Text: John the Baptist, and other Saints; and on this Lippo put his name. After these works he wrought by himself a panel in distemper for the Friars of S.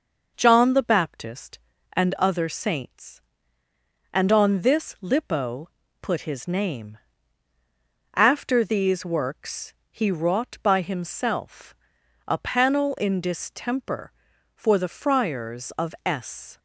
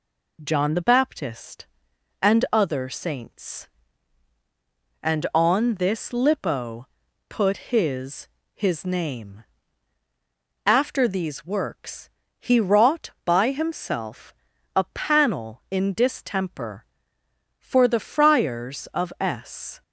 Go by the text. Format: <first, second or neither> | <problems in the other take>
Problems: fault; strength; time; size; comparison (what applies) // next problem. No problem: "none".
first | pauses between "Lippo" and "put"; at 6.8 s; 0.42 s long; slight in the first // says "his" twice; at 8.5 s // pauses between "works" and "he"; slight; at 12.0 s; 0.32 s long; slight in the first // pauses between "himself" and "a"; at 14.3 s; 0.42 s long; noticeable in the first